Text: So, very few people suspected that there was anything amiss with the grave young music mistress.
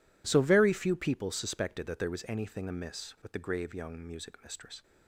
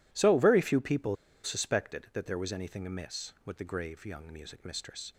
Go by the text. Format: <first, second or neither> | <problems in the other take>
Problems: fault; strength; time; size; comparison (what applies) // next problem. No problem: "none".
first | pauses between "people" and "suspected"; slight; at 1.1 s; 0.28 s long